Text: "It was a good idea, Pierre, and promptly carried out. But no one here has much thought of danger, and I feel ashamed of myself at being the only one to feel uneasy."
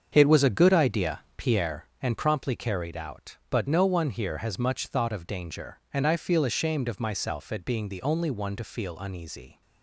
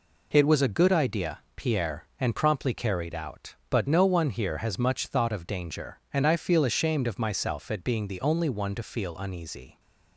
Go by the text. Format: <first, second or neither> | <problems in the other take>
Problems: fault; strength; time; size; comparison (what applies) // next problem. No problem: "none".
second | starts louder than the rest; until 1.7 s; 7 dB